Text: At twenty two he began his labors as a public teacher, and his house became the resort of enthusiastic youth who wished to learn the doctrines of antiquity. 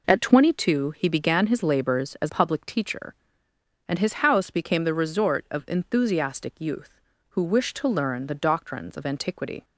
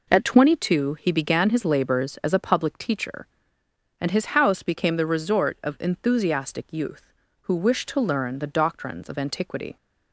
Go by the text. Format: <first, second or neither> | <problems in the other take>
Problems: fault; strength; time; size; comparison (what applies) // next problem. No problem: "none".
second | skips "a"; at 2.2 s